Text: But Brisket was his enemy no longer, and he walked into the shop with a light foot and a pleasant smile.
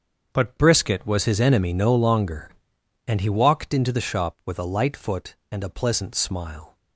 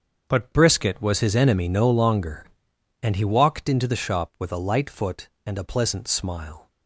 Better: neither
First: starts louder than the rest; until 1.3 s; 7 dB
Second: starts louder than the rest; until 1.3 s; 7 dB

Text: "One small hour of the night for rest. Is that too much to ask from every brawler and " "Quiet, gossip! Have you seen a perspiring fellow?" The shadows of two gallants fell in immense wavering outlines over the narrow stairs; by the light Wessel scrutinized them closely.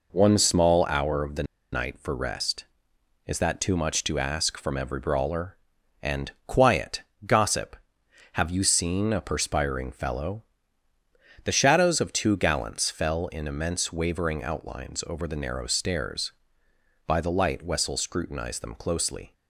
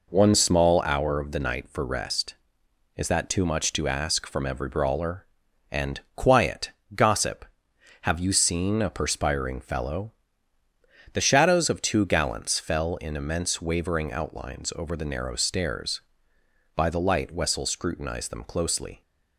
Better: second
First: pauses between "the" and "night"; slight; at 1.4 s; 0.28 s long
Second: none

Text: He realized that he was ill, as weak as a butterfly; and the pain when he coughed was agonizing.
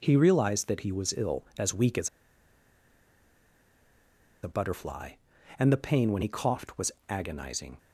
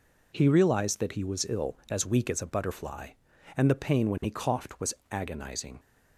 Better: second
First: pauses between "as" and "a"; strong; at 2.0 s; 2.3 s long // pauses between "was" and "agonizing"; slight; at 6.9 s; 0.18 s long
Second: pauses between "was" and "agonizing"; slight; at 4.9 s; 0.18 s long

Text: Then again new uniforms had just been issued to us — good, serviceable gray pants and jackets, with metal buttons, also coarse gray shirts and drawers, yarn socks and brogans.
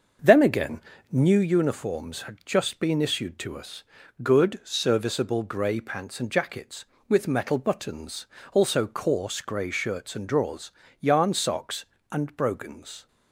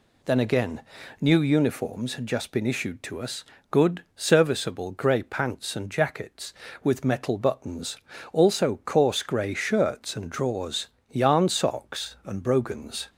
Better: second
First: starts louder than the rest; until 1.5 s; 6 dB // pauses between "again" and "new"; slight; at 0.8 s; 0.30 s long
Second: pauses between "again" and "new"; at 0.8 s; 0.38 s long

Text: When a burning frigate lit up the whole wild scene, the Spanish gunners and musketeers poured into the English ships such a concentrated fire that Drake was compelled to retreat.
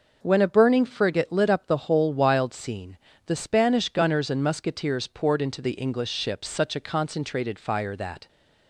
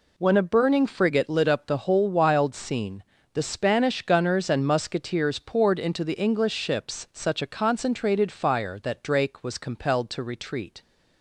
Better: second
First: stops before "Drake was compelled to retreat"; at 8.2 s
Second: none

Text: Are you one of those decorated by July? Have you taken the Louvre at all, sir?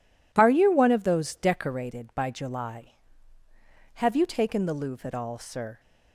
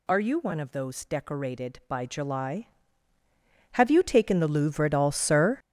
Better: first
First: none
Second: gets louder; strong; throughout; 11.5 dB

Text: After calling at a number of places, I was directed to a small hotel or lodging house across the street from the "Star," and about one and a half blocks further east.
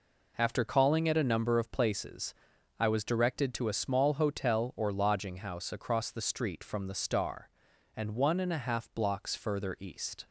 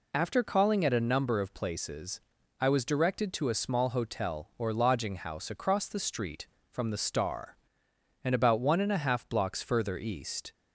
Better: second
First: skips "about"; at 8.1 s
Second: none

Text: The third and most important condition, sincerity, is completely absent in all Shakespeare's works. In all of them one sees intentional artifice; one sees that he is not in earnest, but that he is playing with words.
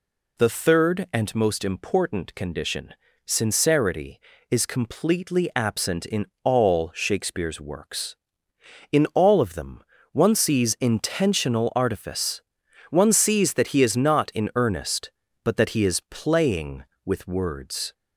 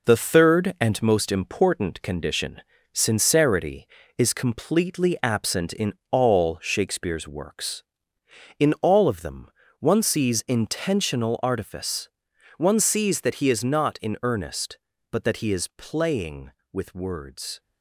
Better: first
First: pauses between "in" and "all"; slight; at 6.2 s; 0.18 s long // pauses between "them" and "one"; slight; at 9.8 s; 0.30 s long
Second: gets quieter; noticeable; throughout; 6 dB // pauses between "in" and "all"; slight; at 5.9 s; 0.18 s long // pauses between "them" and "one"; slight; at 9.4 s; 0.30 s long

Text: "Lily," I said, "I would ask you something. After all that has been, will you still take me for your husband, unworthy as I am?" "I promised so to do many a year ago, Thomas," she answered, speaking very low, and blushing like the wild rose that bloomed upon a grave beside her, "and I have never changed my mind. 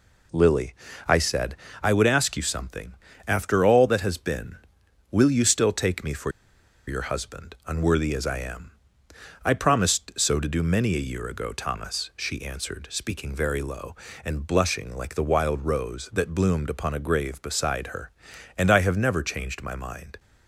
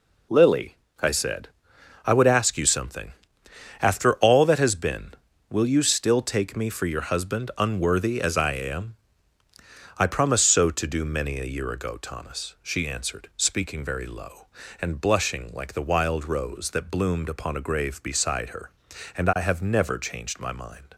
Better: second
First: pauses between "for" and "your"; noticeable; at 6.3 s; 0.56 s long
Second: none

